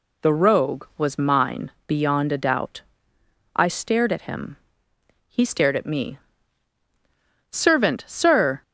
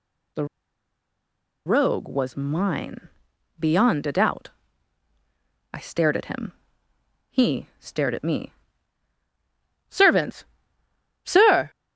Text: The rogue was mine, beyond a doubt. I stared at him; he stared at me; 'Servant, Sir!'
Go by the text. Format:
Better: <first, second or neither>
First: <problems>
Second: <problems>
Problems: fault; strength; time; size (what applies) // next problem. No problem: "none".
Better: first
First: none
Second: pauses between "The" and "rogue"; at 0.4 s; 1.2 s long